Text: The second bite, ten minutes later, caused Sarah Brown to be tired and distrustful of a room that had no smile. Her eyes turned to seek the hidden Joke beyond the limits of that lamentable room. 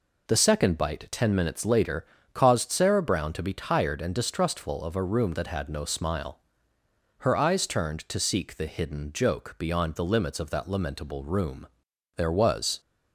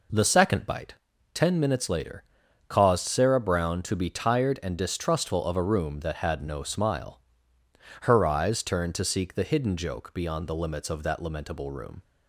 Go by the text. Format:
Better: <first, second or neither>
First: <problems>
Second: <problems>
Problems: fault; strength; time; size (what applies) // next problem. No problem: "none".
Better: second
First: goes on to say "There was"; noticeable; from 12.1 s on; 0.64 s long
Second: none